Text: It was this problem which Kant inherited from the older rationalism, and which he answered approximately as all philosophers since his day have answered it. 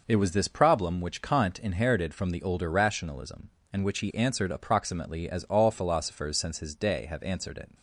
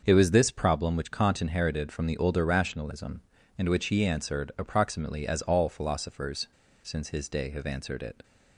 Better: first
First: none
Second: starts louder than the rest; until 1.0 s; 6.5 dB // pauses between "philosophers" and "since"; slight; at 6.4 s; 0.35 s long

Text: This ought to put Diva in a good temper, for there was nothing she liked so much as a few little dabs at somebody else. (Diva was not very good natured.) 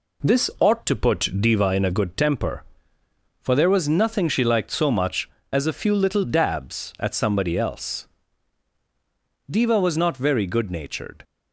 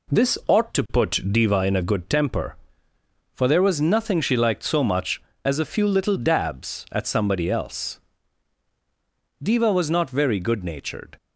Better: neither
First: none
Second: none

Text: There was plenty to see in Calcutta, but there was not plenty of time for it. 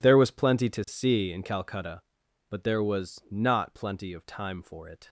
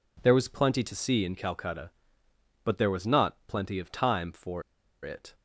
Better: first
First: none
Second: pauses between "for" and "it"; at 4.6 s; 0.42 s long

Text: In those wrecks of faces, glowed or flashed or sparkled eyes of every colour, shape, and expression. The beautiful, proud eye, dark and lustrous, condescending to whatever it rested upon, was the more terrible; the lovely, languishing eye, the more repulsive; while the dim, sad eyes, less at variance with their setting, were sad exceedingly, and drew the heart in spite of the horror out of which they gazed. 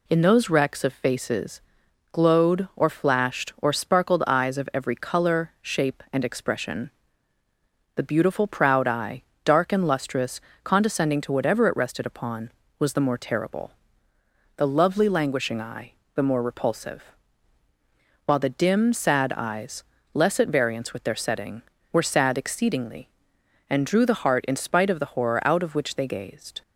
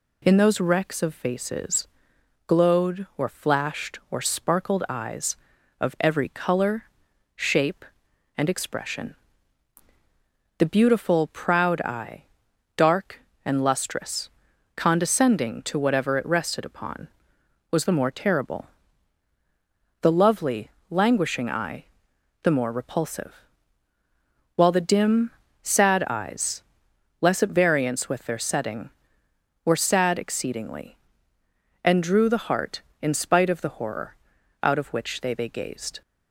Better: first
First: none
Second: pauses between "horror" and "out"; noticeable; at 34.1 s; 0.48 s long // says "they" twice; at 35.3 s

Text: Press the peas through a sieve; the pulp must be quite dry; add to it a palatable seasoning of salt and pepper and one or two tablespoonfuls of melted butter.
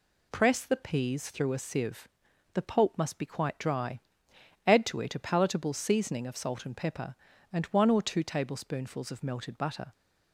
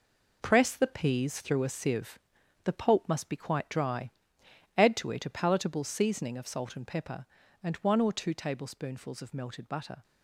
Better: first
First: none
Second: gets quieter; strong; throughout; 8.5 dB

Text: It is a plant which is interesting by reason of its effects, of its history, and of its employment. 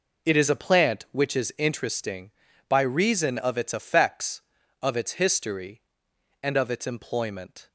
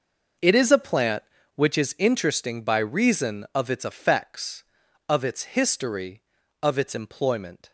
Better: first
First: none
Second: skips "and"; at 6.4 s

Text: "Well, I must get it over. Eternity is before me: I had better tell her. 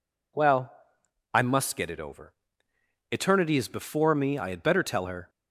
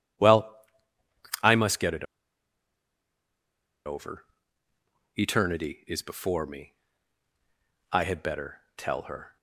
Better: first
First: none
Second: pauses between "it" and "over"; strong; at 2.0 s; 1.8 s long

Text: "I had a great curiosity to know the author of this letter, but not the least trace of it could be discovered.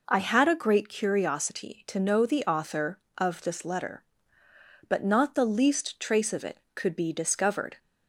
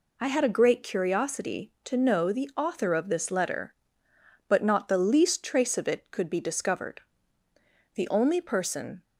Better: first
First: none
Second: goes on to say "The only person"; noticeable; from 7.9 s on; 1.0 s long

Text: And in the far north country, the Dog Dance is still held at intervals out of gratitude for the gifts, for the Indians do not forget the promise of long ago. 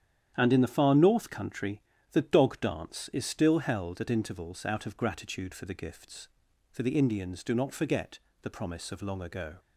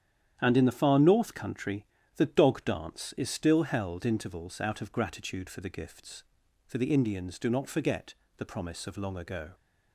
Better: first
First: starts louder than the rest; strong; until 1.3 s; 9.5 dB // pauses between "forget" and "the"; slight; at 8.1 s; 0.22 s long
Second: starts louder than the rest; strong; until 1.4 s; 9.5 dB // skips "at"; at 4.0 s // pauses between "forget" and "the"; slight; at 8.1 s; 0.22 s long

